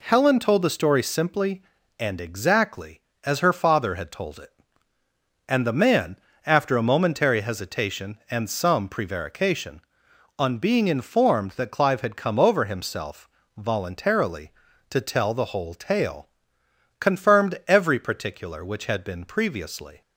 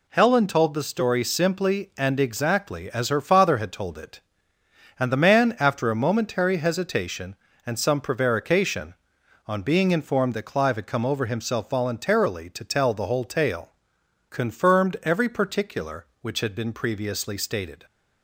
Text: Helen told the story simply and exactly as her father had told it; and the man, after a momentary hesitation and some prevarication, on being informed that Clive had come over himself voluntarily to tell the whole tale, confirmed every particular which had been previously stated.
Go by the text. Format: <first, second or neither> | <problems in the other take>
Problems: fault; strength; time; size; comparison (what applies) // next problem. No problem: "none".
second | pauses between "himself" and "voluntarily"; slight; at 13.2 s; 0.26 s long // stops before "stated"; at 20.0 s